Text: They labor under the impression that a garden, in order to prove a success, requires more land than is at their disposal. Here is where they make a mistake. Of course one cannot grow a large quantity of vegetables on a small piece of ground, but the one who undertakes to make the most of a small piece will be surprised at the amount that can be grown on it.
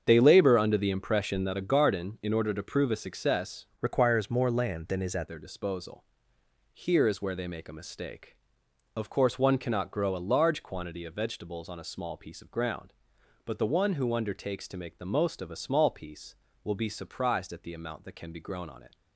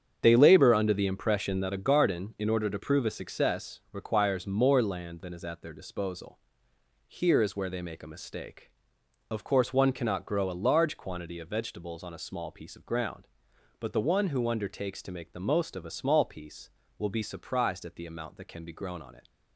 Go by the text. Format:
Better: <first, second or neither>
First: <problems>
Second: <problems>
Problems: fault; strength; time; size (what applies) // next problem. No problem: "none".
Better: second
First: starts louder than the rest; strong; until 1.0 s; 7.5 dB // changes voice from "requires" to "at"; from 3.8 to 5.2 s; 1.4 s long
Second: starts louder than the rest; strong; until 1.2 s; 8 dB